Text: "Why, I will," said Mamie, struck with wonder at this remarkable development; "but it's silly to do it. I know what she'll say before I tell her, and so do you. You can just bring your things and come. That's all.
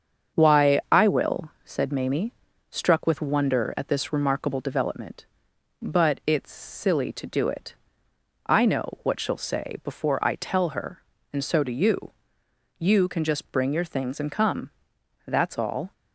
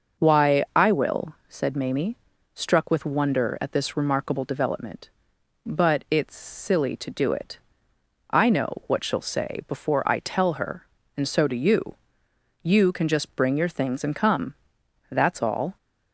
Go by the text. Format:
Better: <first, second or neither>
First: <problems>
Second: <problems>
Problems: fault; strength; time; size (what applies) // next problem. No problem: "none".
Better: second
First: gets quieter; noticeable; throughout; 5 dB // starts louder than the rest; strong; until 1.4 s; 7 dB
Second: starts louder than the rest; until 1.2 s; 6 dB